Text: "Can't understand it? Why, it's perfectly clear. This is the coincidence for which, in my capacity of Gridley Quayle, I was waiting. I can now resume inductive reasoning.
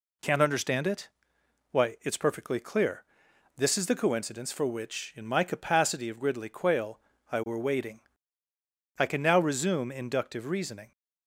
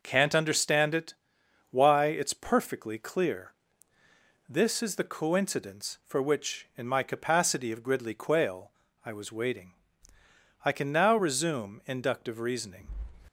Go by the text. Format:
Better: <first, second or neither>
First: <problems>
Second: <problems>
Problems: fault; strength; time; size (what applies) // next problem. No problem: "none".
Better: second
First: says "were" for "was"; at 7.4 s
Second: none